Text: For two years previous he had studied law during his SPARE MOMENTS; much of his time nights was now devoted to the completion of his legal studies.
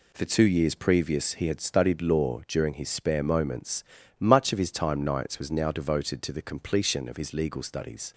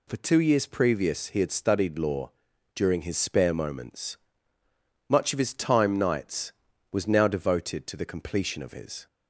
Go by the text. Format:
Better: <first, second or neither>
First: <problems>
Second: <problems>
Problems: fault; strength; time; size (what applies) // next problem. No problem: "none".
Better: first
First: none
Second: pauses between "law" and "during"; at 2.3 s; 0.44 s long // stops before "legal studies"; at 9.0 s